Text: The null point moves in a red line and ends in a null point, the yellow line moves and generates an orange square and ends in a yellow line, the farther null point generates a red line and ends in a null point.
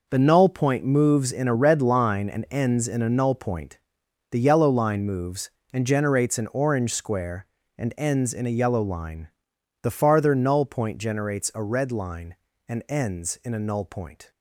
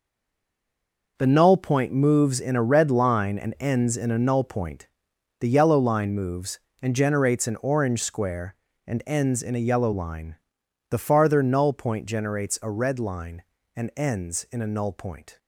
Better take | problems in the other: first | stays silent before the first word; noticeable; until 1.1 s; 1.1 s long

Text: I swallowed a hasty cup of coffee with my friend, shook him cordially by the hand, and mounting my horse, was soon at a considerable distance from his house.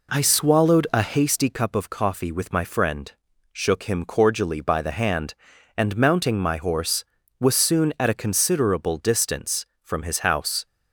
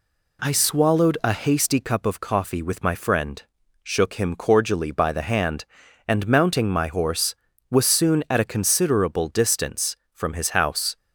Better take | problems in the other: second | starts louder than the rest; until 1.2 s; 3.5 dB

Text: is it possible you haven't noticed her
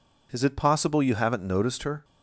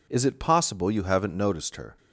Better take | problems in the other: neither | none

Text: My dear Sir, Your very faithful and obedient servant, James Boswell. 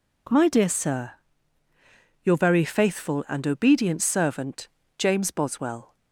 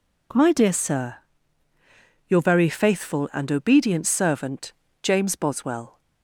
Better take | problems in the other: neither | none

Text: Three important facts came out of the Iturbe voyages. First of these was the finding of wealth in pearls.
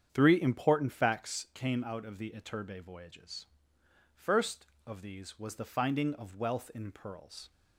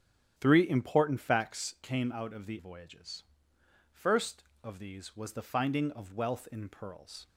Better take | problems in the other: first | starts louder than the rest; strong; until 1.3 s; 9 dB; strong in the first // skips "Iturbe"; at 2.5 s

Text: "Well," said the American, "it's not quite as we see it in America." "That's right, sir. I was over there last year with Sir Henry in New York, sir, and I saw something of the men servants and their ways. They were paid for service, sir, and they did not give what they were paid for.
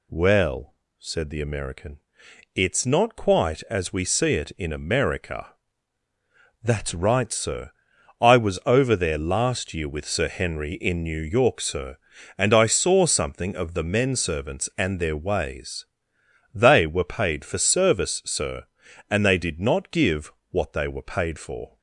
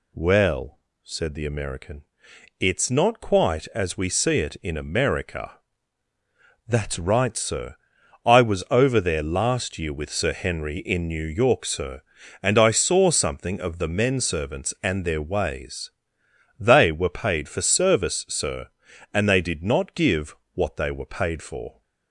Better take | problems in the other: neither | pauses between "give" and "what"; slight; the same in both

